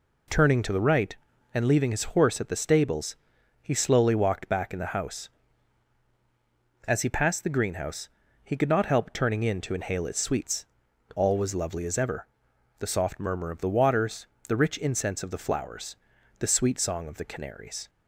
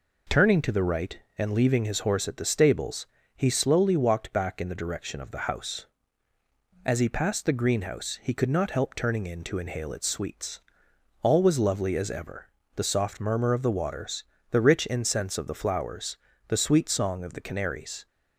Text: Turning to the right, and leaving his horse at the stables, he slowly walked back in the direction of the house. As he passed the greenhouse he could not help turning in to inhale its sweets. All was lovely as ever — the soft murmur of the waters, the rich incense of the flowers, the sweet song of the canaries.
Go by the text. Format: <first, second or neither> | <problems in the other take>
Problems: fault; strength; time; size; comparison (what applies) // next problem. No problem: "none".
second | skips "direction of the"; at 4.9 s // pauses between "greenhouse" and "he"; slight; at 8.0 s; 0.34 s long